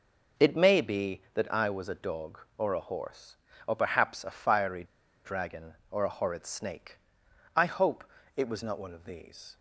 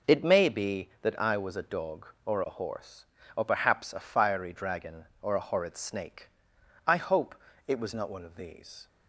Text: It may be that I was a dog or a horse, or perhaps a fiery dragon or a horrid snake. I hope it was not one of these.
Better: second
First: pauses between "fiery" and "dragon"; at 4.8 s; 0.40 s long // pauses between "hope" and "it"; slight; at 8.0 s; 0.34 s long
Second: pauses between "hope" and "it"; slight; at 7.3 s; 0.34 s long

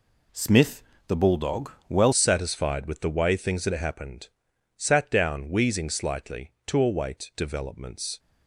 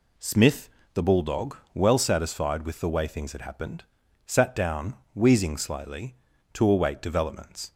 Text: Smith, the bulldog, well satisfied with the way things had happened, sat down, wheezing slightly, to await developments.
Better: second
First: changes voice at "satisfied"; from 2.1 s on; 6.0 s long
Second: none

